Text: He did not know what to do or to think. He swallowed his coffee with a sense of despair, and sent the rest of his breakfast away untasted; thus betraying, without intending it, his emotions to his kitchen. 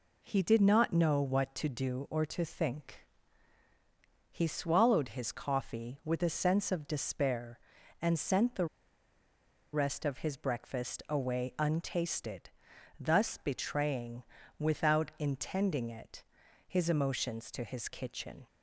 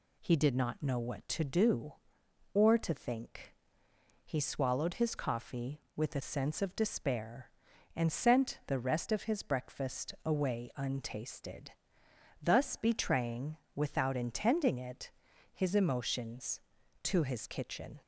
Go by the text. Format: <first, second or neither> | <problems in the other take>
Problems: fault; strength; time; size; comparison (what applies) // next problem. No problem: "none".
second | pauses between "the" and "rest"; at 8.6 s; 1.0 s long